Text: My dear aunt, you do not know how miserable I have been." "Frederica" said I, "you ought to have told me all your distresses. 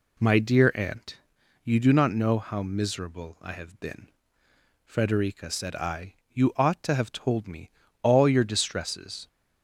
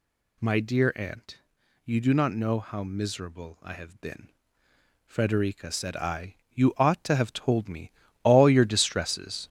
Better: first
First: pauses between "me" and "all"; slight; at 7.6 s; 0.32 s long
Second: gets louder; noticeable; throughout; 6 dB // pauses between "me" and "all"; slight; at 7.8 s; 0.32 s long

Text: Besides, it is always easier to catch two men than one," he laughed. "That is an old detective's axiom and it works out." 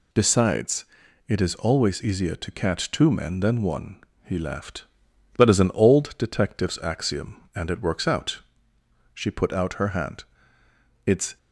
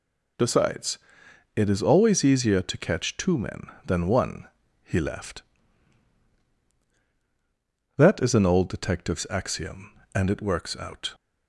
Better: second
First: goes on to say "She put out her hand It's"; strong; from 9.1 s on; 2.2 s long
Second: none

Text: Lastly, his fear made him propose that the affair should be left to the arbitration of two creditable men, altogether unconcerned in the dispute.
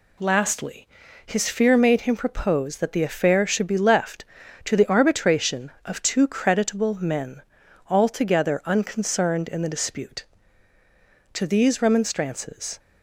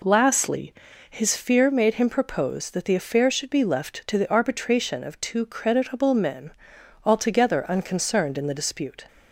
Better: second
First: goes on to say "To these remonstrances"; from 11.3 s on; 1.4 s long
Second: none

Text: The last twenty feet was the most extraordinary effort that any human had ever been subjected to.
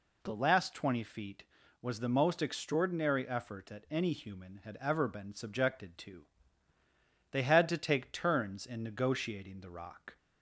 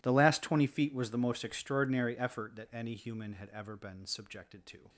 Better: second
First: goes on to say "They had to take turns in negotiating the rock"; strong; from 7.3 s on; 2.8 s long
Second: none

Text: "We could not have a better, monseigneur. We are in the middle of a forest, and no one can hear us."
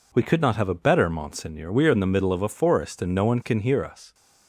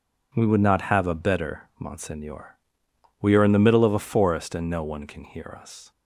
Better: first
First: none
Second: says "would" for "could"; at 0.4 s

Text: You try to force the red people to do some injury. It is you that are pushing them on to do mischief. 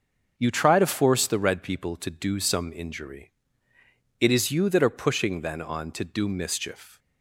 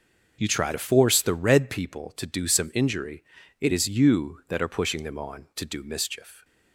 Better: second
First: starts louder than the rest; until 1.3 s; 6.5 dB // says "then" for "them"; at 5.4 s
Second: none

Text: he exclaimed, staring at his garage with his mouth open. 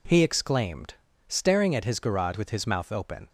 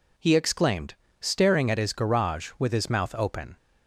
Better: neither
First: none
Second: none

